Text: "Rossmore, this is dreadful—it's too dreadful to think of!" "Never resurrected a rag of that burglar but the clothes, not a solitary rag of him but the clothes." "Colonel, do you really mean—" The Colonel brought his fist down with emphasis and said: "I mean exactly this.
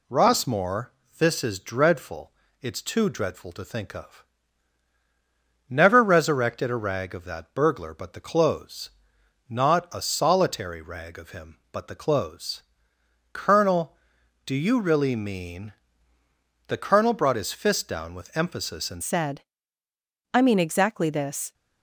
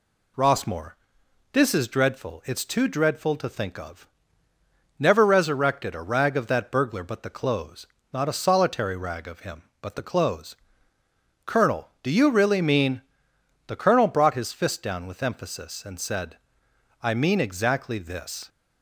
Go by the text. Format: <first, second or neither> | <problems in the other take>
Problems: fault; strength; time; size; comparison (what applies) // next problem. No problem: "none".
second | changes voice at "said"; from 19.0 s on; 2.5 s long